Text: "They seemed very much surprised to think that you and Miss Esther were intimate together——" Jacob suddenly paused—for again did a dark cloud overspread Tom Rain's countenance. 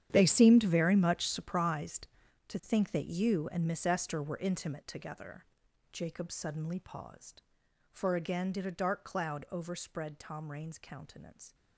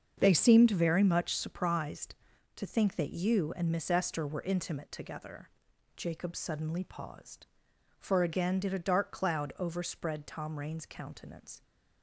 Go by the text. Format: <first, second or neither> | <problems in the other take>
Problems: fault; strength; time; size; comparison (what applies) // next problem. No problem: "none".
second | gets quieter; strong; throughout; 16.5 dB // starts louder than the rest; strong; until 1.1 s; 10 dB; also in the second